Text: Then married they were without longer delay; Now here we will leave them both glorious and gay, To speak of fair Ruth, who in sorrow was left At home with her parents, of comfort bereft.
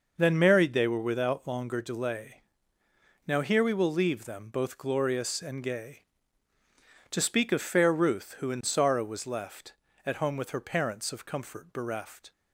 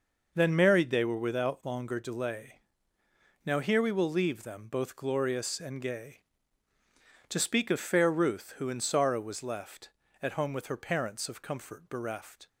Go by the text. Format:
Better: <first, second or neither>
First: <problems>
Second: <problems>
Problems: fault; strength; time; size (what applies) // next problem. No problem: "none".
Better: neither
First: none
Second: none